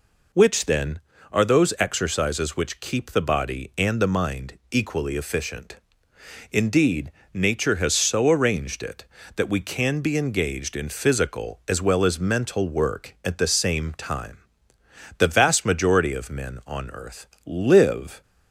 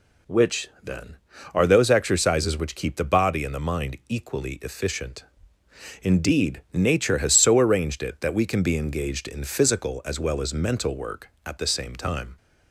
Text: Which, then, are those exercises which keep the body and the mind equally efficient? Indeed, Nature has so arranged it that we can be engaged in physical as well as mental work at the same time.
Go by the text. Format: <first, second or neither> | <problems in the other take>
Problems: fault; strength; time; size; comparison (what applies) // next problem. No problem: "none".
second | goes on to say "The vast majority of men on earth live"; strong; from 15.1 s on; 3.0 s long